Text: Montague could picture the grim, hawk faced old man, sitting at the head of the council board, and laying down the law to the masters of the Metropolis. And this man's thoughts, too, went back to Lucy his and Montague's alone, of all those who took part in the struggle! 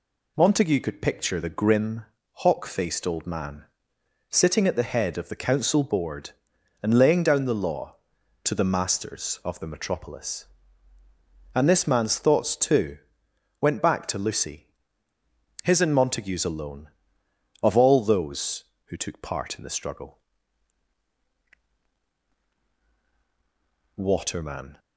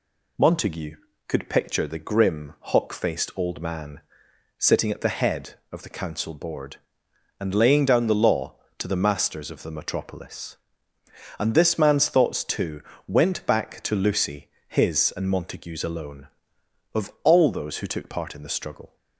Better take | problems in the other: second | pauses between "Lucy" and "his"; at 14.6 s; 1.0 s long; slight in the second // goes on to say "Waterman"; noticeable; from 23.9 s on; 0.82 s long

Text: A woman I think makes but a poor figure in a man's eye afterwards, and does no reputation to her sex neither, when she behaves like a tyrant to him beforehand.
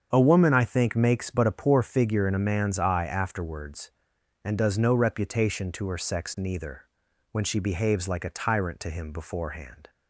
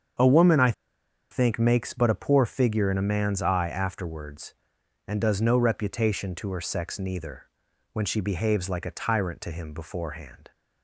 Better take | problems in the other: first | starts louder than the rest; strong; until 1.7 s; 7.5 dB; strong in the first // pauses between "I" and "think"; noticeable; at 0.7 s; 0.59 s long

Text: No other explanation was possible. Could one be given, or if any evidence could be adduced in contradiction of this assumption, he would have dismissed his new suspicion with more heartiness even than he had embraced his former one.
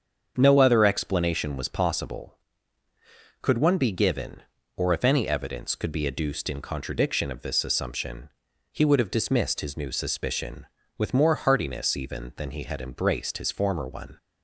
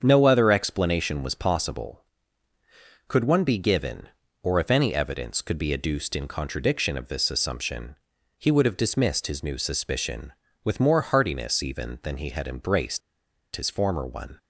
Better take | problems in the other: first | starts louder than the rest; strong; until 1.0 s; 7 dB; also in the first // pauses between "embraced" and "his"; noticeable; at 13.0 s; 0.55 s long

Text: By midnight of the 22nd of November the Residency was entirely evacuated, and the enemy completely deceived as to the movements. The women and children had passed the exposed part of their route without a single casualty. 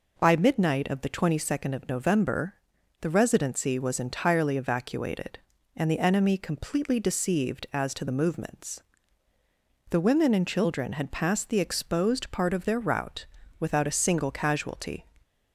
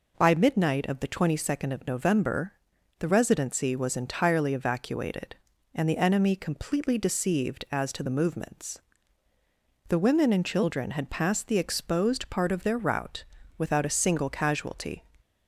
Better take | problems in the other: neither | pauses between "November" and "the"; noticeable; the same in both // pauses between "route" and "without"; slight; the same in both

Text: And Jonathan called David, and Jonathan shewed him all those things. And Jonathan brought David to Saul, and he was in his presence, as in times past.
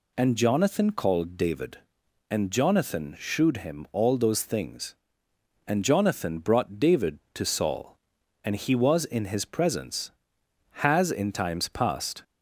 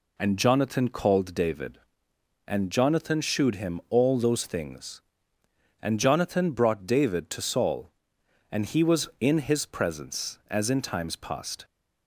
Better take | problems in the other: second | says "has" for "as"; at 10.8 s

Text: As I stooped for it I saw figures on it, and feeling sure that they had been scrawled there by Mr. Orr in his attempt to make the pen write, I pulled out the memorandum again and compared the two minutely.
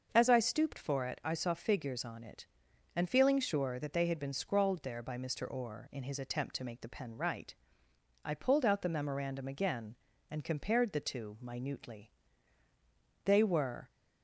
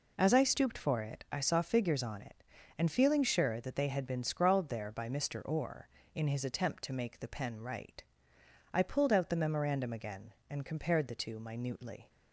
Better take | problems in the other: second | starts louder than the rest; until 1.1 s; 6.5 dB // goes on to say "They were"; noticeable; from 13.2 s on; 0.64 s long

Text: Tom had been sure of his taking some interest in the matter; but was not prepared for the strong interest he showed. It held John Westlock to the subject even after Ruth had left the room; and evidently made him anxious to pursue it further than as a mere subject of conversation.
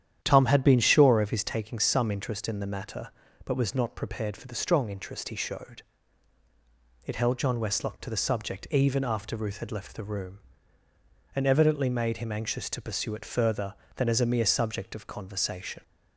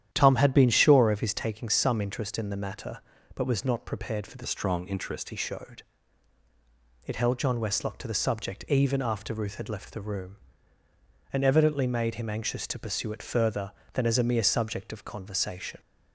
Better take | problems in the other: first | starts louder than the rest; strong; until 1.1 s; 10.5 dB; strong in the first // changes voice from "strong" to "interest"; from 4.4 to 5.2 s; 0.8 s long

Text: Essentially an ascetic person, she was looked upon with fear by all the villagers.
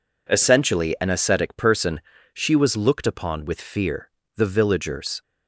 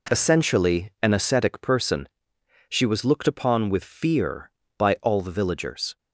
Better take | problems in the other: second | skips "by all"; at 4.2 s

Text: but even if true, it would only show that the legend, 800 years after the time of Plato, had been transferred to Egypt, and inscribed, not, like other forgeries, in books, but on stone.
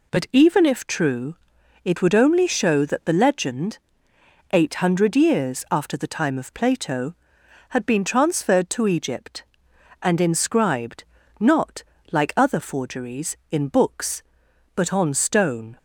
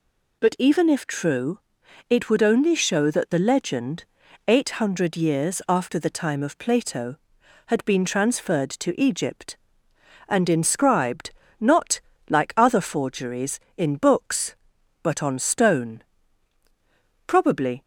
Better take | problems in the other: first | goes on to say "Probably"; from 17.2 s on; 0.56 s long

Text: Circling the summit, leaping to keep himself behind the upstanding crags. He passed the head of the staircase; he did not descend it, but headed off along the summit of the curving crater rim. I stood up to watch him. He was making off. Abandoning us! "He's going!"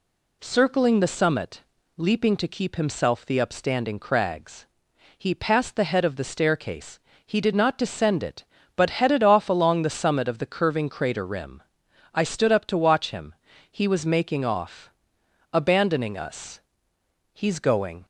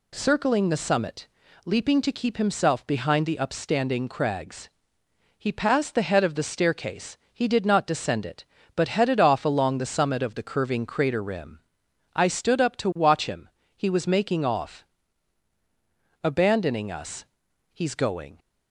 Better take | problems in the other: second | skips "behind"; at 3.2 s

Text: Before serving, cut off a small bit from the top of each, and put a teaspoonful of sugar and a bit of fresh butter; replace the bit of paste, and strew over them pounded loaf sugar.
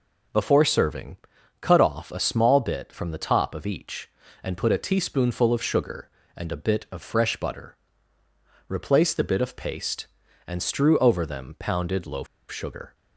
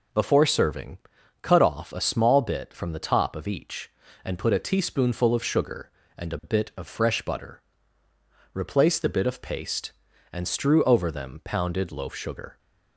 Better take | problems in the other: second | pauses between "loaf" and "sugar"; slight; at 12.2 s; 0.24 s long

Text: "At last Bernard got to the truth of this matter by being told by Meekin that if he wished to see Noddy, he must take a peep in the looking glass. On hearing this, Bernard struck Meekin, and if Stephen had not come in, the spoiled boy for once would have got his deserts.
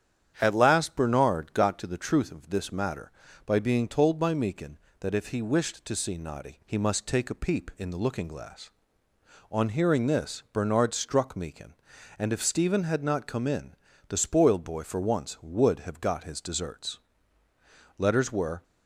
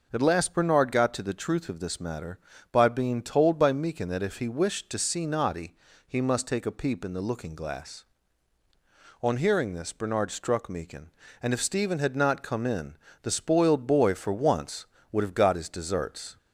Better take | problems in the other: second | starts louder than the rest; strong; until 1.4 s; 9 dB // goes on to say "Letters were"; noticeable; from 17.9 s on; 0.66 s long

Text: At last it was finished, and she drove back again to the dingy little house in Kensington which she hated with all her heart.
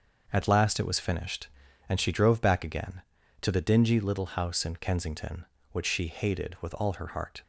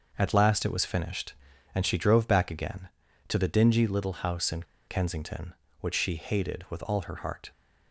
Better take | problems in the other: first | starts louder than the rest; noticeable; until 1.1 s; 6 dB; also in the first // pauses between "in" and "Kensington"; slight; at 4.6 s; 0.24 s long

